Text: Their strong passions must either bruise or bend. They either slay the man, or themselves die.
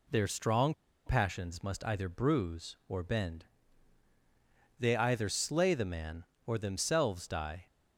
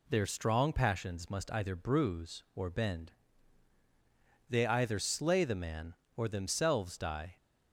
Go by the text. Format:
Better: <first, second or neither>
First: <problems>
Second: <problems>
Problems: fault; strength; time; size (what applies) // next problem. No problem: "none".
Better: second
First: pauses between "strong" and "passions"; slight; at 0.7 s; 0.34 s long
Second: none